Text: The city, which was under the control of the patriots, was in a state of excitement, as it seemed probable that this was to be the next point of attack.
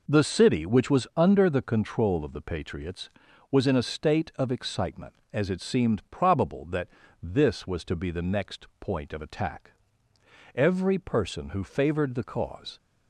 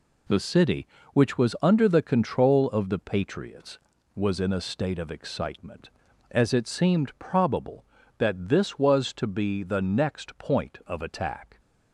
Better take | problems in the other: second | pauses between "that" and "this"; slight; at 6.8 s; 0.34 s long // goes on to say "Every person who favored the cause"; strong; from 10.5 s on; 2.2 s long

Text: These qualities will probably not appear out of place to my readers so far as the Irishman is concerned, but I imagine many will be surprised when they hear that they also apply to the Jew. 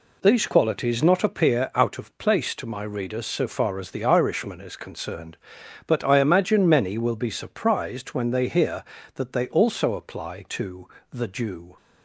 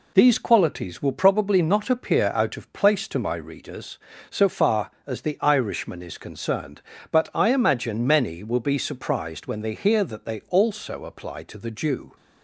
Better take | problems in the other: second | skips "will probably"; at 1.0 s // pauses between "to" and "the"; slight; at 10.8 s; 0.24 s long

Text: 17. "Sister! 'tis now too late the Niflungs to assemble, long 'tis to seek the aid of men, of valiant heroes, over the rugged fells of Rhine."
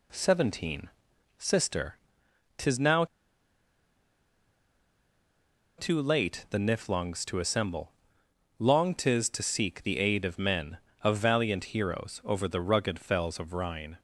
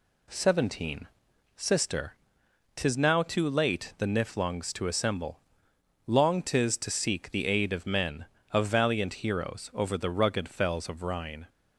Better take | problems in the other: second | pauses between "now" and "too"; strong; at 3.0 s; 2.7 s long

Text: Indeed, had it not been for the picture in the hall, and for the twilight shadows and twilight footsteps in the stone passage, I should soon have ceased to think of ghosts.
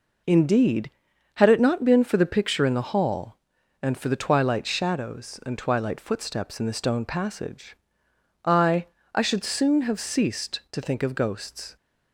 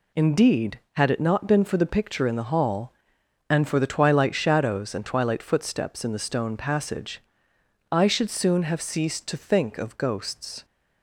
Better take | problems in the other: second | says "I" twice; at 9.1 s

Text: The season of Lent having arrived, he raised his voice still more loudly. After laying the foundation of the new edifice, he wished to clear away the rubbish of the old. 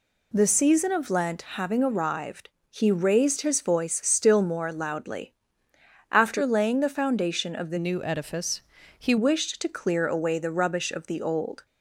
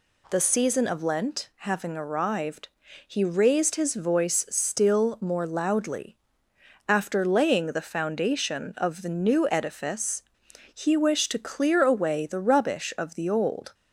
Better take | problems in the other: second | changes voice from "new" to "he"; from 7.7 to 9.1 s; 1.4 s long

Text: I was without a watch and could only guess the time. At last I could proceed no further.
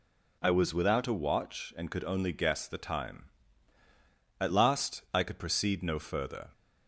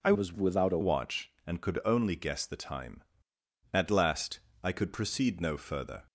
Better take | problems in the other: first | changes voice from "was" to "a"; from 0.1 to 0.7 s; 0.6 s long // pauses between "last" and "I"; slight; at 4.4 s; 0.22 s long

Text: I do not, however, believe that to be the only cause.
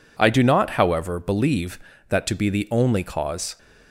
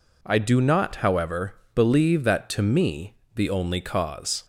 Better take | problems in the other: first | says "me" for "be"; at 2.6 s

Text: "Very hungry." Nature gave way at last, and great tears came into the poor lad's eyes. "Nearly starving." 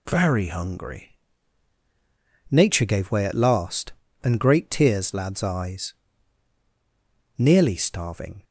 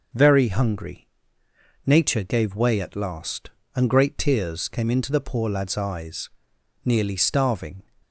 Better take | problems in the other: second | skips "came into the poor"; at 5.1 s

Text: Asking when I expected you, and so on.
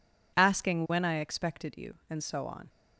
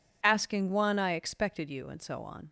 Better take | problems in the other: first | says "one" for "when"; at 0.6 s

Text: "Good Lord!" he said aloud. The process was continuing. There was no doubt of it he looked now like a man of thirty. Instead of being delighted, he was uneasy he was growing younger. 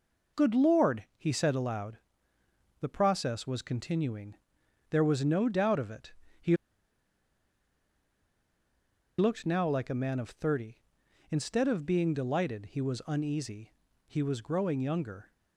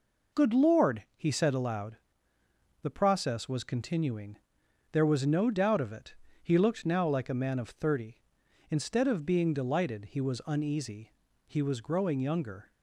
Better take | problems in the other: second | pauses between "it" and "he"; slight; at 6.1 s; 0.26 s long; slight in the second // pauses between "he" and "looked"; strong; at 6.5 s; 2.6 s long // pauses between "uneasy" and "he"; slight; at 13.7 s; 0.34 s long; slight in the second

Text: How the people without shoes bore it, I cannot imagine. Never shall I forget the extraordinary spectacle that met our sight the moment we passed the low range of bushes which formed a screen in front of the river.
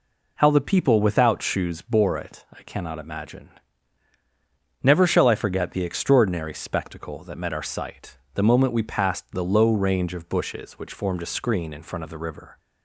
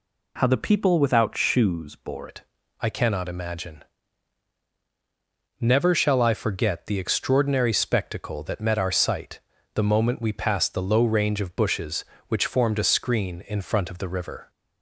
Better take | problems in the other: first | changes voice at "it"; from 2.2 s on; 12.2 s long // pauses between "sight" and "the"; slight; at 9.3 s; 0.34 s long; slight in the first

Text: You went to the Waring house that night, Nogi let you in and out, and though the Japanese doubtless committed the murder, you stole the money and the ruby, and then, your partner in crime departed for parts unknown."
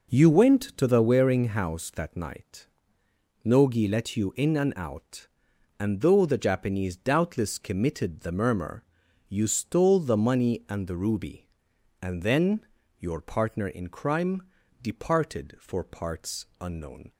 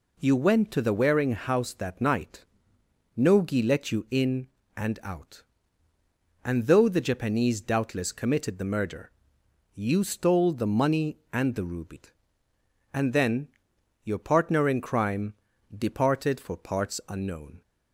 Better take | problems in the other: second | says "murmur" for "murder"; at 8.3 s // pauses between "crime" and "departed"; at 14.4 s; 0.40 s long; also in the second

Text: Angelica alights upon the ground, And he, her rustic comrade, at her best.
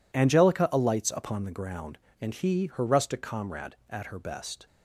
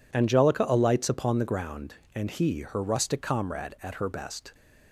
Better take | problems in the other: neither | none

